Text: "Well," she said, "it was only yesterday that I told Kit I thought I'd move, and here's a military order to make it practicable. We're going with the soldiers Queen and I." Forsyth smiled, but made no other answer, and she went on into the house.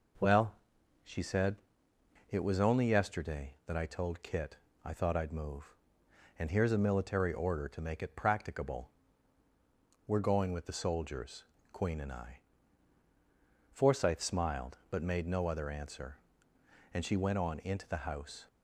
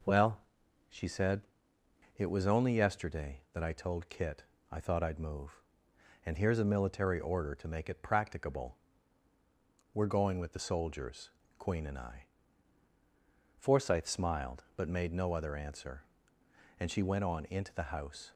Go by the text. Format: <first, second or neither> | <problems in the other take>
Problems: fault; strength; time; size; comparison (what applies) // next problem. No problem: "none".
neither | pauses between "Kit" and "I"; slight; the same in both // pauses between "soldiers" and "Queen"; slight; the same in both